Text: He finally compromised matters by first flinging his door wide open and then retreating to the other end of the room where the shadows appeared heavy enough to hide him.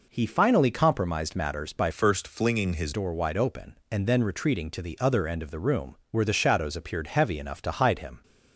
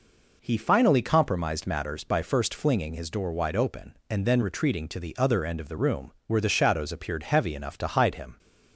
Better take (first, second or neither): second